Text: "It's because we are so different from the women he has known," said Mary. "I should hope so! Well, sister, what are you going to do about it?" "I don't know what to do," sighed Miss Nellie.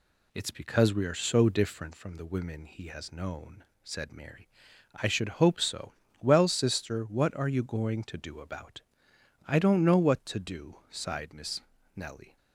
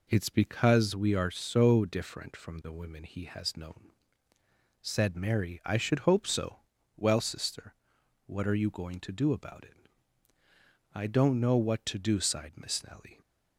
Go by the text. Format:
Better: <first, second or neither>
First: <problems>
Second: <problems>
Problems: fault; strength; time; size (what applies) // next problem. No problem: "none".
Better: second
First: skips "it"; at 9.1 s // pauses between "Miss" and "Nellie"; slight; at 11.6 s; 0.34 s long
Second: none